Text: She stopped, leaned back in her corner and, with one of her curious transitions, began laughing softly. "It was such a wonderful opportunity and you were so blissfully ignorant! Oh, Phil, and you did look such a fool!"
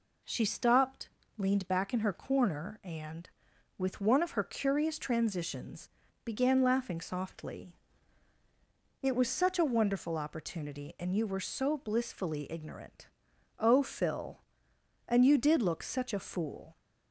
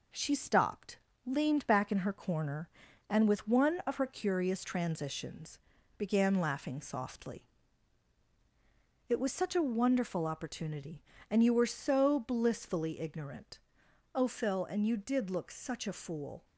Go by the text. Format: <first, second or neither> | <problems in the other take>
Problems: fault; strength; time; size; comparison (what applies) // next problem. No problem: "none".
first | gets quieter; slight; throughout; 3 dB